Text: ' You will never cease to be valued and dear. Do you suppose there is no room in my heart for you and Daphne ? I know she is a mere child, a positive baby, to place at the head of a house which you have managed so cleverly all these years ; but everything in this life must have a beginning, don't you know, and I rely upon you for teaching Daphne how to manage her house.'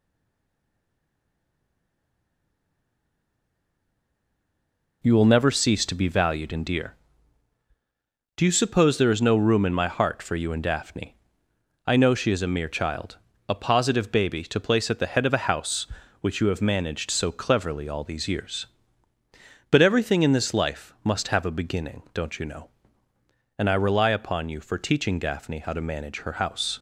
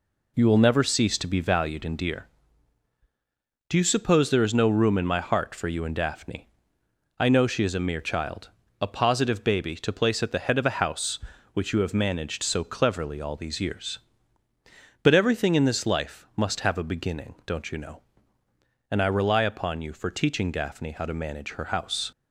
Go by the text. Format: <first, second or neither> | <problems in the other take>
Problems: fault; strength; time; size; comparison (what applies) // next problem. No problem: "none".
second | stays silent before the first word; strong; until 5.0 s; 5.0 s long